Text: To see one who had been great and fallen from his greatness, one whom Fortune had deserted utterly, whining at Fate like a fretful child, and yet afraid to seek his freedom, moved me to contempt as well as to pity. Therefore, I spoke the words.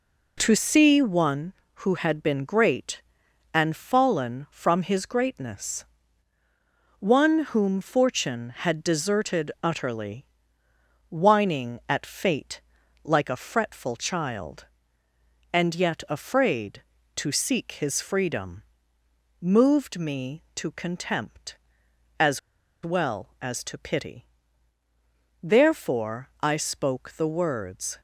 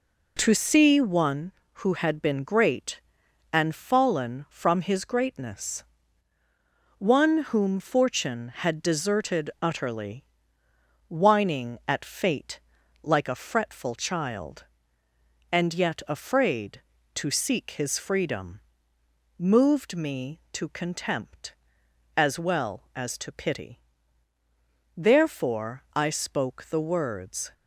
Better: second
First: pauses between "Fate" and "like"; at 12.6 s; 0.42 s long // pauses between "as" and "well"; at 22.3 s; 0.44 s long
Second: pauses between "Fate" and "like"; at 12.5 s; 0.42 s long

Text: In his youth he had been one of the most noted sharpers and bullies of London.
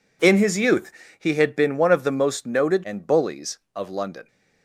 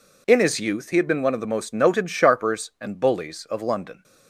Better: second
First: pauses between "youth" and "he"; slight; at 0.9 s; 0.26 s long // skips "sharpers"; at 2.8 s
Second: none

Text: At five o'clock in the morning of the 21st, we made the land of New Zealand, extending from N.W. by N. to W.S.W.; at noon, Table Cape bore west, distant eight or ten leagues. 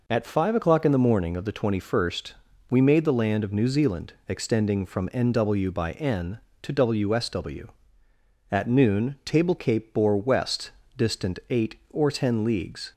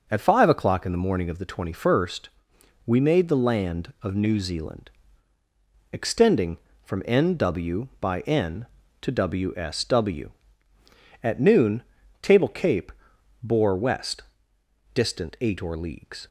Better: first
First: none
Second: pauses between "Cape" and "bore"; noticeable; at 12.9 s; 0.50 s long // skips "ten"; at 15.7 s

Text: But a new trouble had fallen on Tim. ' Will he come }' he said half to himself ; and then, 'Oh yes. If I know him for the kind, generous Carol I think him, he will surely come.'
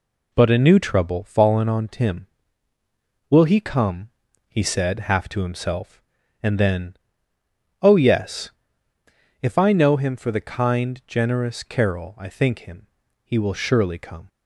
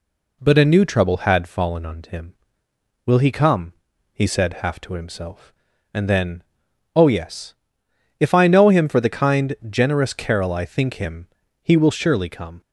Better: second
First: skips "had"; at 1.2 s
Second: none

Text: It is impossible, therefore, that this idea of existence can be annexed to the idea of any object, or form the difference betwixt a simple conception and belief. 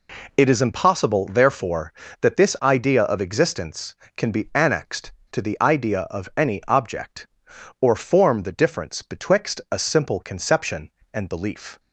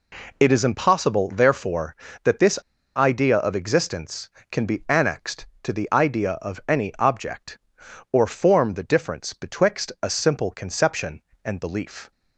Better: first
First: none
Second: pauses between "this" and "idea"; at 2.5 s; 0.37 s long

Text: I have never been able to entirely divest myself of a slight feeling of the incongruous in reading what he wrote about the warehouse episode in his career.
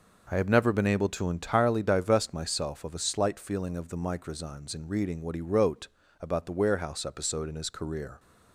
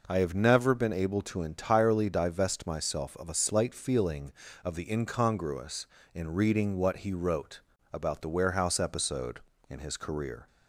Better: second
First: says "microzymes" for "incongruous"; at 3.9 s // pauses between "wrote" and "about"; slight; at 5.8 s; 0.32 s long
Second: pauses between "wrote" and "about"; slight; at 7.6 s; 0.32 s long

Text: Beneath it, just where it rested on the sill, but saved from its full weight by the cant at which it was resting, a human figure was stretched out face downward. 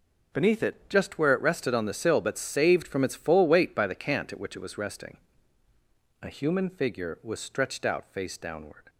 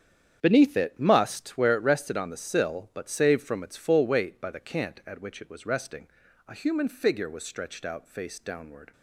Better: first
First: none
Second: starts louder than the rest; strong; until 1.4 s; 8.5 dB // says "must" for "just"; at 0.9 s

